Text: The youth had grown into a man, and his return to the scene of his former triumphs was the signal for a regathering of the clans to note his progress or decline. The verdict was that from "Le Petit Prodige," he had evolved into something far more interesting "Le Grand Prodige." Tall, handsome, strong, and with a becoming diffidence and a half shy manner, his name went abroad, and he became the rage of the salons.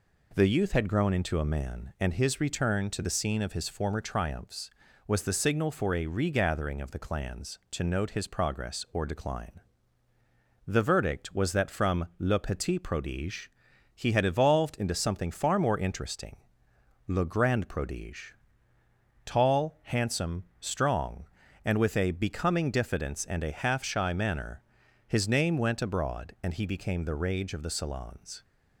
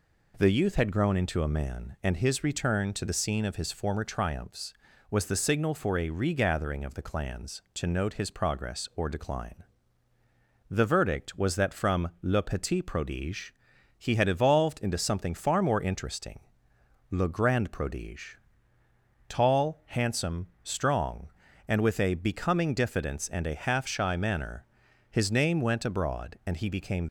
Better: first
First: pauses between "interesting" and "Le"; noticeable; at 16.3 s; 0.70 s long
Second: pauses between "interesting" and "Le"; noticeable; at 16.4 s; 0.70 s long // stops before "the rage of the salons"; at 27.0 s

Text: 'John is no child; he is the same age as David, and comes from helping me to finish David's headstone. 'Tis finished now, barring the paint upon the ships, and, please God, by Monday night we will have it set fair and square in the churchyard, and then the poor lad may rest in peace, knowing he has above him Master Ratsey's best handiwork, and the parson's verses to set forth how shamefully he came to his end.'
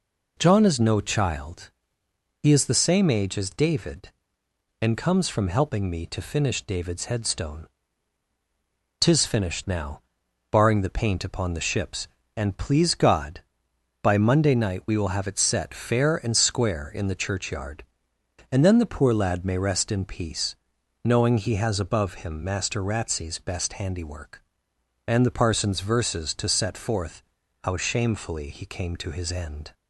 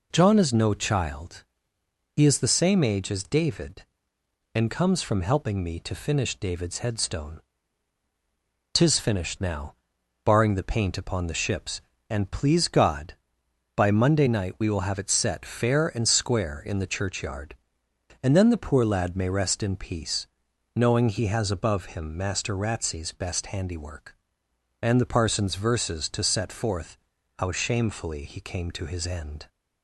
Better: neither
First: pauses between "forth" and "how"; at 27.2 s; 0.42 s long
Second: pauses between "forth" and "how"; at 26.9 s; 0.42 s long

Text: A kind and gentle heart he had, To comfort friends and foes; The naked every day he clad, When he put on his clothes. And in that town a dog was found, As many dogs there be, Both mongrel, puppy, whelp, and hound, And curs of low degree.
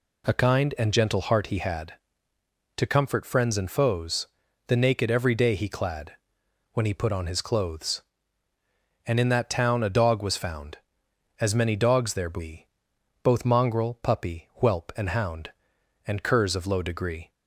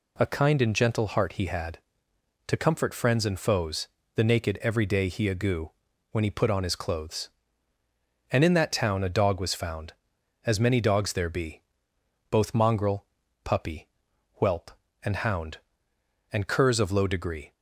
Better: first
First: none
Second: says "agoo" for "clad"; at 5.2 s

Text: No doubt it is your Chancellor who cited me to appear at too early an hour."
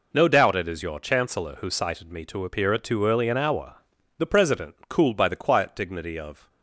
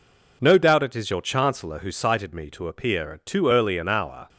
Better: second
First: goes on to say "The President cooled by the quiet dignity of"; strong; from 4.1 s on; 2.3 s long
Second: none

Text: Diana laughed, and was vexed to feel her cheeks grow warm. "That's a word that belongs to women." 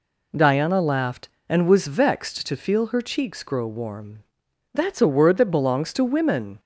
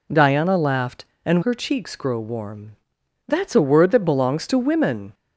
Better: first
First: none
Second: skips "was vexed to feel"; at 1.4 s

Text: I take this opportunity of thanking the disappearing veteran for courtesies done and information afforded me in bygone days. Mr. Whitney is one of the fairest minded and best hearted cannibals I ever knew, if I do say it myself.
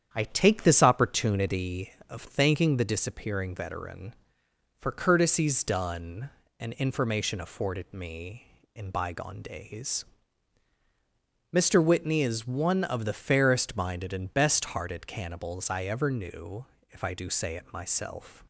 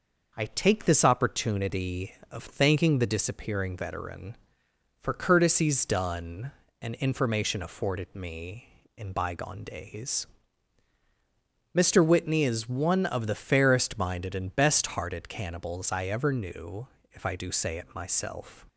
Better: second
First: starts louder than the rest; strong; until 1.7 s; 9 dB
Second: none

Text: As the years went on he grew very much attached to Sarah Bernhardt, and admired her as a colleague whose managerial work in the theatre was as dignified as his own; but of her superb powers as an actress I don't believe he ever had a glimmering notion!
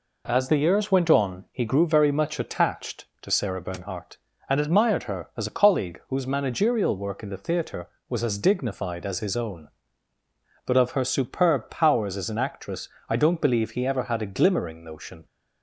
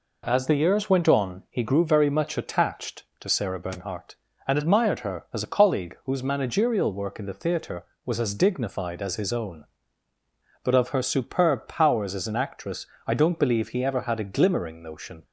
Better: neither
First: pauses between "actress" and "I"; slight; at 12.8 s; 0.18 s long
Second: pauses between "actress" and "I"; slight; at 12.8 s; 0.18 s long

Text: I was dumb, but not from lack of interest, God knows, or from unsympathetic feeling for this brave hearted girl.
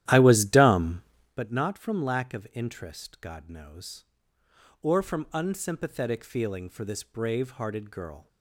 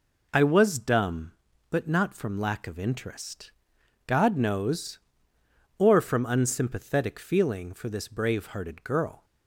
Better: second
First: starts louder than the rest; strong; until 1.4 s; 12.5 dB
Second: none

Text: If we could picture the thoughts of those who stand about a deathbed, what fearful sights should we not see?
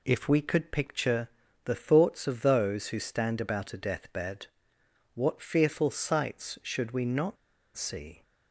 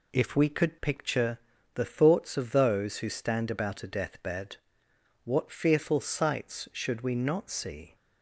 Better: second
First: pauses between "picture" and "the"; slight; at 1.2 s; 0.36 s long // pauses between "not" and "see"; at 7.3 s; 0.39 s long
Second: pauses between "picture" and "the"; slight; at 1.3 s; 0.36 s long

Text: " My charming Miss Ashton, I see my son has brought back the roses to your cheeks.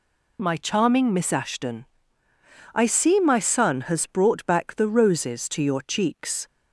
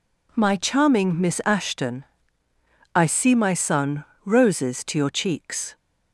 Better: first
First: none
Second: skips "has brought back the"; at 4.1 s

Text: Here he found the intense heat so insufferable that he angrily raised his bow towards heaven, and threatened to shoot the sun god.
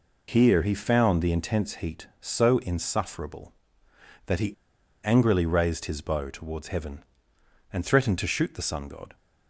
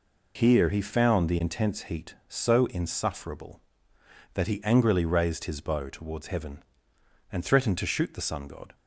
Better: second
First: pauses between "he" and "angrily"; noticeable; at 4.5 s; 0.48 s long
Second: none

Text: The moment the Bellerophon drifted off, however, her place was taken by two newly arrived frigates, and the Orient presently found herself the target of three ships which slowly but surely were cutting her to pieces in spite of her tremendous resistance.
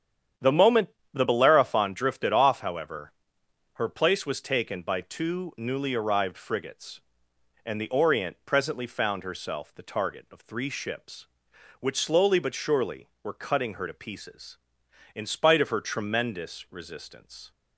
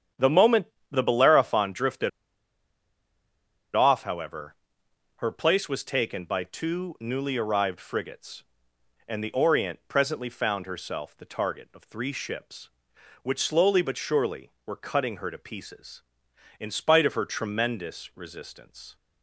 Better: first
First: starts louder than the rest; strong; until 1.6 s; 9 dB // pauses between "moment" and "the"; slight; at 0.8 s; 0.26 s long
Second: starts louder than the rest; strong; until 1.4 s; 9 dB // pauses between "moment" and "the"; slight; at 0.6 s; 0.26 s long // pauses between "drifted" and "off"; strong; at 2.0 s; 1.6 s long

